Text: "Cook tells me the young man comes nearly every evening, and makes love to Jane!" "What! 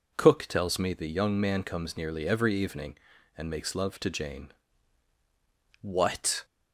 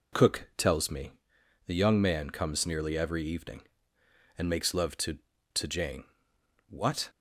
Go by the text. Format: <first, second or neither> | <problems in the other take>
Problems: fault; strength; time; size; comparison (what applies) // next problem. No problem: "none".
first | pauses between "me" and "the"; noticeable; at 1.1 s; 0.54 s long // says "to" twice; at 5.5 s